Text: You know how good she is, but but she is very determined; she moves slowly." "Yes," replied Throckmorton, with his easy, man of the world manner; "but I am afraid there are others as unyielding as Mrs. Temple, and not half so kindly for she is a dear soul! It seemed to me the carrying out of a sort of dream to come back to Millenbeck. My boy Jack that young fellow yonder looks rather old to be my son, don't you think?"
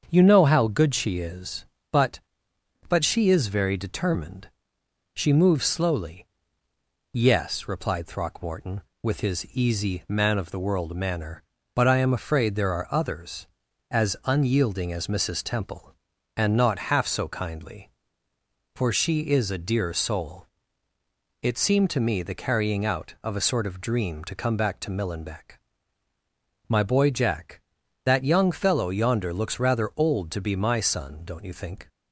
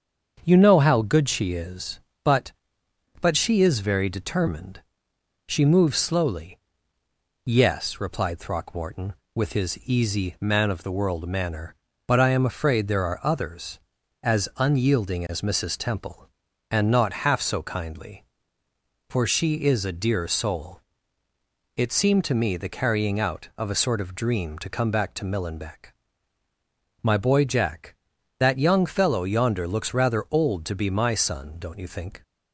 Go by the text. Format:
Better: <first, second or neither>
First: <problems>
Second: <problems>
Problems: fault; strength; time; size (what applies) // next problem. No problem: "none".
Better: neither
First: starts louder than the rest; until 1.1 s; 7 dB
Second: starts louder than the rest; until 1.4 s; 7 dB